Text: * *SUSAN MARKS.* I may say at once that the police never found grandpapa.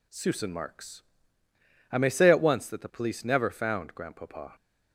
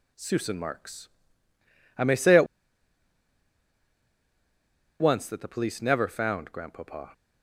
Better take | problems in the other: first | pauses between "at" and "once"; strong; at 2.4 s; 2.5 s long

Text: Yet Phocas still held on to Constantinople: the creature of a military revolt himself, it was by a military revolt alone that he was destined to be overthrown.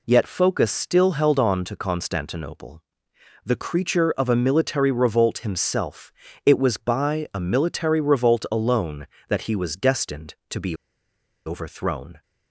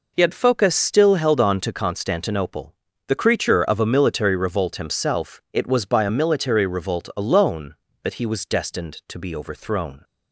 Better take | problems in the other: second | pauses between "be" and "overthrown"; noticeable; at 10.7 s; 0.70 s long

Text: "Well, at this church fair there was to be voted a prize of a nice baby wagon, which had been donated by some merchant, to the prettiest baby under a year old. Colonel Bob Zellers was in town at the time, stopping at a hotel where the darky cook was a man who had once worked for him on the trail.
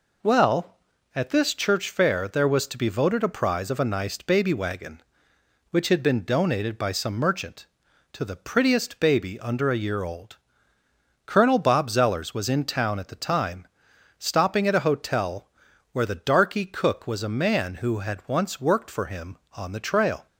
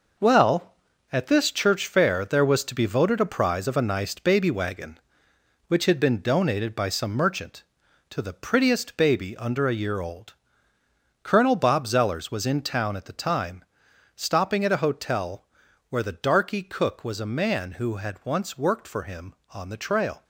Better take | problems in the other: first | gets quieter; strong; throughout; 8 dB // pauses between "hotel" and "where"; at 15.4 s; 0.44 s long; also in the first

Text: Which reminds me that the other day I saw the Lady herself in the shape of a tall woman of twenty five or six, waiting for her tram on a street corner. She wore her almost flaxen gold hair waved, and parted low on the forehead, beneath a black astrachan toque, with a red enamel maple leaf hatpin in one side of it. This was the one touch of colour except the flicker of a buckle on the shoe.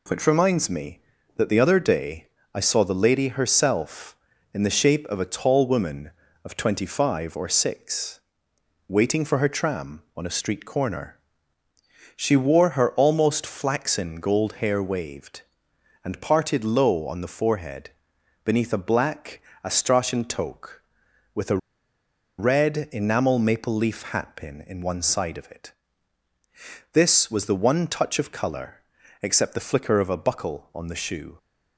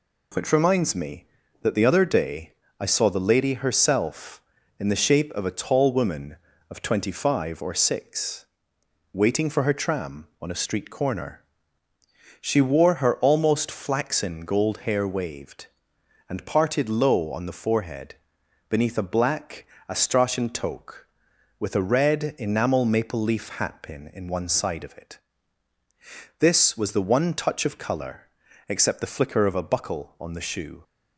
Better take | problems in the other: second | pauses between "day" and "I"; slight; at 2.2 s; 0.28 s long; slight in the second // pauses between "black" and "astrachan"; slight; at 19.4 s; 0.24 s long; slight in the second // pauses between "a" and "red"; noticeable; at 21.5 s; 0.81 s long // pauses between "colour" and "except"; at 28.8 s; 0.40 s long; also in the second

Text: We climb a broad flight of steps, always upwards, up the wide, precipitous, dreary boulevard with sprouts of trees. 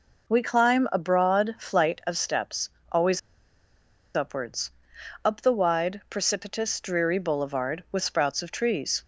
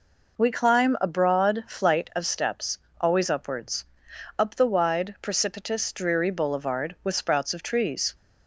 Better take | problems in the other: second | pauses between "always" and "upwards"; noticeable; at 3.1 s; 0.95 s long

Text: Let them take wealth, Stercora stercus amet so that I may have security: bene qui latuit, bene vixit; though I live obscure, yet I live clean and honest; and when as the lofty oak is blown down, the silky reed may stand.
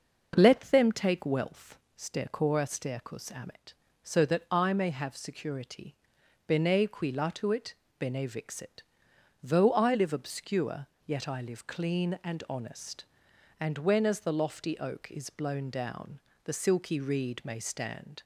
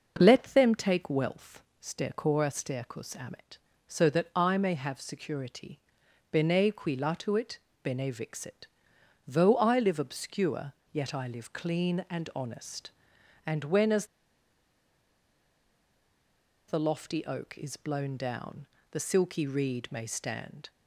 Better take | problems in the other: first | pauses between "as" and "the"; strong; at 14.0 s; 2.6 s long

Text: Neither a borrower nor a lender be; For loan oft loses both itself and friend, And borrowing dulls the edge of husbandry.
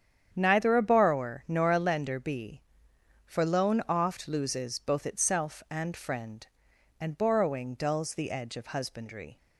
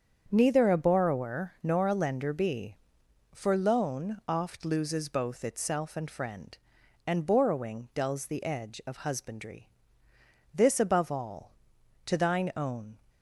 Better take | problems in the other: first | starts louder than the rest; strong; until 1.3 s; 7.5 dB; strong in the first // goes on to say "This above all to thine own"; strong; from 10.5 s on; 2.4 s long

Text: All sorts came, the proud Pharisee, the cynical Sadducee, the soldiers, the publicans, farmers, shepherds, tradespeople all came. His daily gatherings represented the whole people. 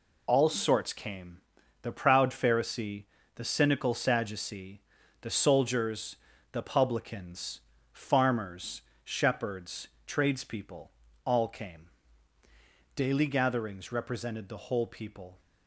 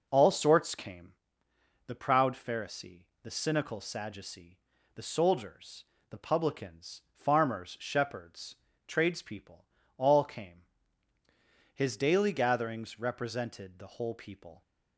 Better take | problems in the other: second | pauses between "tradespeople" and "all"; slight; at 10.9 s; 0.34 s long; slight in the second // skips "His"; at 12.4 s

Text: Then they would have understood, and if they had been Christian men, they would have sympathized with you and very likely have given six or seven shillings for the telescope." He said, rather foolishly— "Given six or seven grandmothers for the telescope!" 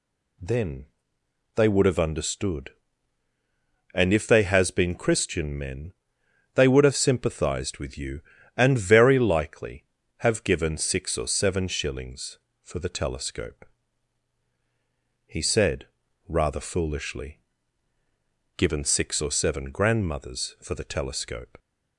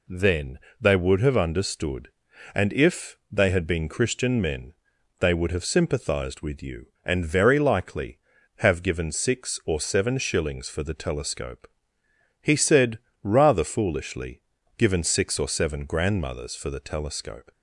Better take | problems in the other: second | pauses between "Then" and "they"; noticeable; at 0.8 s; 0.68 s long; slight in the second // says "has" for "had"; at 4.4 s

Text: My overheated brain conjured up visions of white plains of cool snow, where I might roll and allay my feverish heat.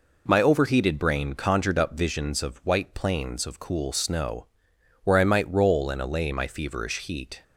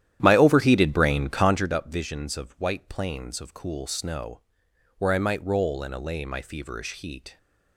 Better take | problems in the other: first | starts louder than the rest; strong; until 1.7 s; 11.5 dB

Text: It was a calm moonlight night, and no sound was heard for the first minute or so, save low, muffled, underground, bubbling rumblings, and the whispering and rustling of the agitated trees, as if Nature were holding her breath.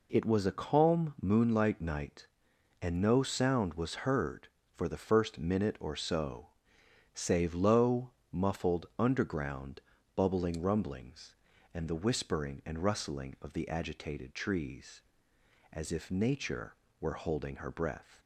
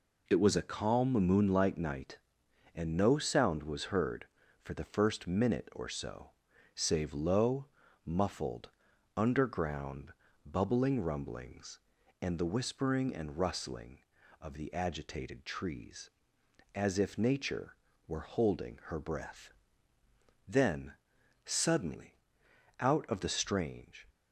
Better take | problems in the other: first | goes on to say "Then suddenly out of the strange"; strong; from 20.4 s on; 3.6 s long

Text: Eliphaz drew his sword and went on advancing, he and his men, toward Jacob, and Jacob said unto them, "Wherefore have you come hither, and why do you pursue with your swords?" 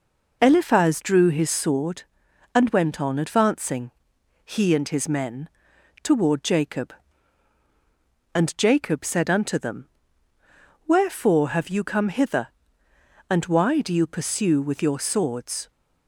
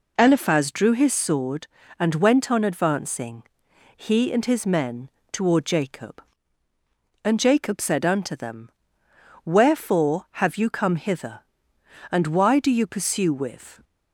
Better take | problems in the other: first | stops before "your swords"; at 13.8 s

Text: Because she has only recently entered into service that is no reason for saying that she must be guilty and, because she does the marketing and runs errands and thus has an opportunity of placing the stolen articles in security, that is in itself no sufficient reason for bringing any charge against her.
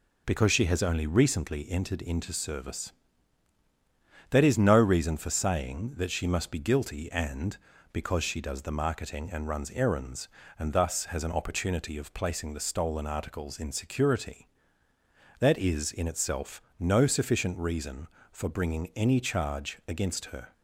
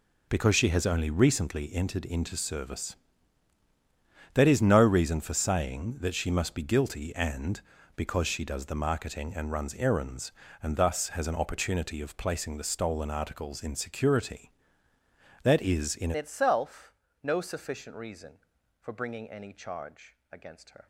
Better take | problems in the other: first | changes voice at "itself"; from 16.1 s on; 4.7 s long // pauses between "itself" and "no"; slight; at 16.9 s; 0.30 s long; slight in the first // pauses between "charge" and "against"; slight; at 20.1 s; 0.16 s long

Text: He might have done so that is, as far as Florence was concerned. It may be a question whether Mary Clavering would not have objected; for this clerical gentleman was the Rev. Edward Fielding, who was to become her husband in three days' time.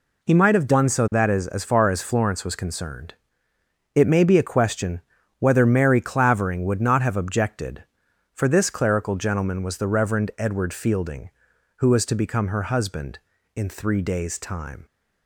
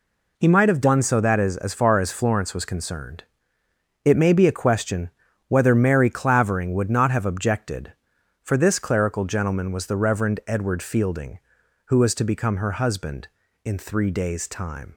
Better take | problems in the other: neither | pauses between "question" and "whether"; the same in both

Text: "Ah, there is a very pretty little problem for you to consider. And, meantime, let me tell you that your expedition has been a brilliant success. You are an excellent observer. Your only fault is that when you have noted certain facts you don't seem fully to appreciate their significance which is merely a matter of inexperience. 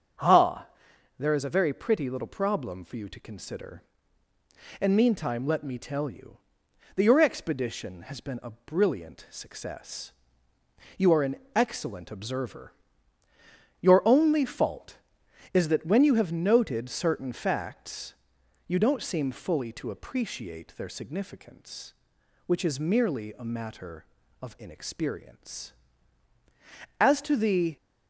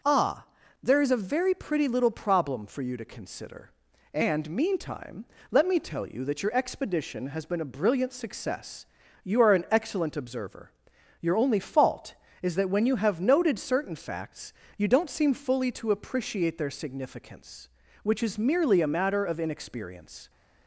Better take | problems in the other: second | starts louder than the rest; until 1.7 s; 7 dB // pauses between "an" and "excellent"; slight; at 11.3 s; 0.18 s long // pauses between "facts" and "you"; noticeable; at 18.1 s; 0.54 s long; slight in the second // goes on to say "As to the"; noticeable; from 26.9 s on; 0.76 s long

